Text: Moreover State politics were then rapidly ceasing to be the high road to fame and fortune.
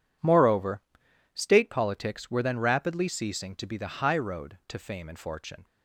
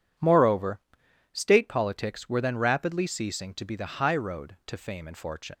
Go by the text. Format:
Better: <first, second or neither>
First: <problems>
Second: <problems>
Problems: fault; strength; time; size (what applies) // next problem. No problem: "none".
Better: first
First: pauses between "Moreover" and "State"; noticeable; at 0.8 s; 0.52 s long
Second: pauses between "Moreover" and "State"; noticeable; at 0.7 s; 0.52 s long // leaves "fortune" unfinished; at 5.5 s; 80 ms